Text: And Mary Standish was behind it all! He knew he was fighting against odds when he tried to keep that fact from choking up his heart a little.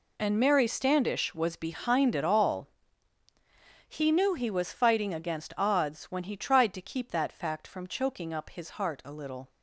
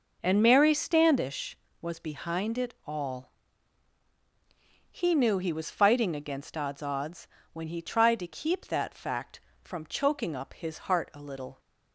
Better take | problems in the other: first | says "odds" twice; at 6.8 s

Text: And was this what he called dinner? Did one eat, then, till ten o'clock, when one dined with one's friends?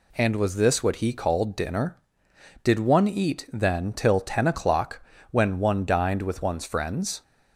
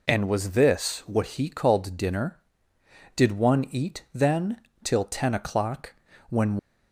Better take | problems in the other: first | stops before "one dined with one's friends"; at 6.5 s

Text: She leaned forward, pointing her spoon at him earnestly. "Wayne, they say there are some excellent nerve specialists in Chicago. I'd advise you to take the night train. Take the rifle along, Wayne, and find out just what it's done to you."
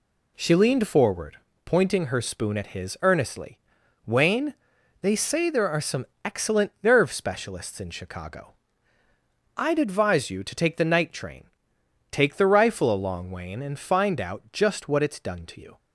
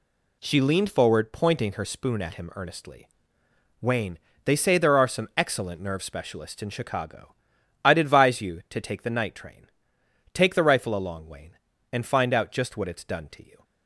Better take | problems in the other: second | says "his" for "him"; at 2.6 s // pauses between "some" and "excellent"; slight; at 6.0 s; 0.18 s long

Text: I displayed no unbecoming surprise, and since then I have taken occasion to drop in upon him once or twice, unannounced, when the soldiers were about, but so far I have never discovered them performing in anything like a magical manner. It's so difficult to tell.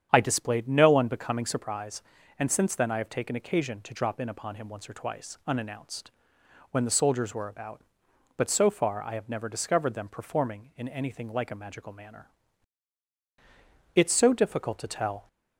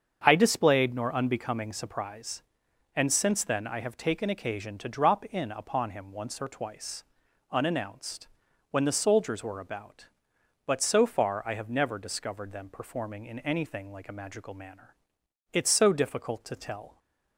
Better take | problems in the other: first | starts louder than the rest; strong; until 1.2 s; 7 dB; strong in the first // says "nor" for "no"; at 0.9 s

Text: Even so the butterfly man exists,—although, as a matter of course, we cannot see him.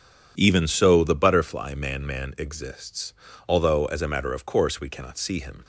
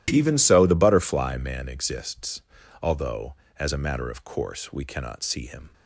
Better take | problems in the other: second | says "man" twice; at 2.0 s

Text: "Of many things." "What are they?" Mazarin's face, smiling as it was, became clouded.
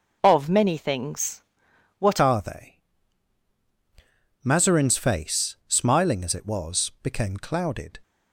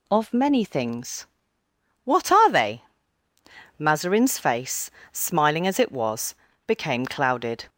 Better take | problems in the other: second | changes voice at "are"; from 2.2 s on; 5.8 s long

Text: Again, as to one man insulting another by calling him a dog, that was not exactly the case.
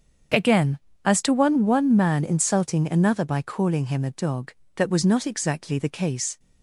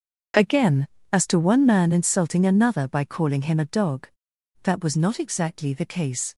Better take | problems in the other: second | starts louder than the rest; until 1.6 s; 7 dB; also in the second // says "one" twice; at 1.6 s

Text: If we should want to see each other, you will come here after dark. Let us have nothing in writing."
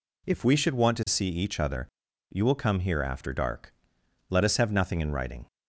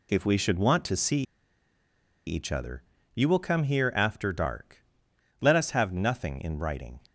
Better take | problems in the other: first | pauses between "see" and "each"; at 1.2 s; 1.0 s long

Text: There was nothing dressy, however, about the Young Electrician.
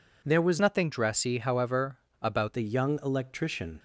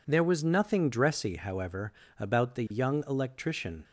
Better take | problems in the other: second | changes voice from "nothing" to "about"; from 0.5 to 2.5 s; 2.0 s long

